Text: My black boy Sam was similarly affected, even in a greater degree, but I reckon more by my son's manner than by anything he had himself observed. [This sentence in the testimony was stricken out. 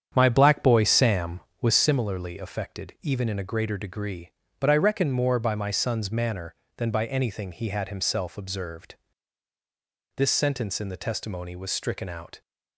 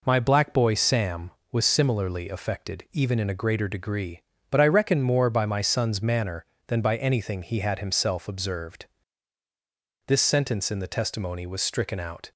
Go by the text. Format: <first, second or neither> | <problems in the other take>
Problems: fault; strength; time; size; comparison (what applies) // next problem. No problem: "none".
second | starts louder than the rest; strong; until 2.0 s; 8.5 dB